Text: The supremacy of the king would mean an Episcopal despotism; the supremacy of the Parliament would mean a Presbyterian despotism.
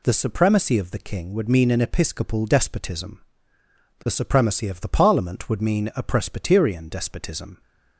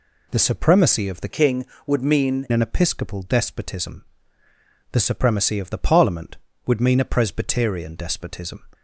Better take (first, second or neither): first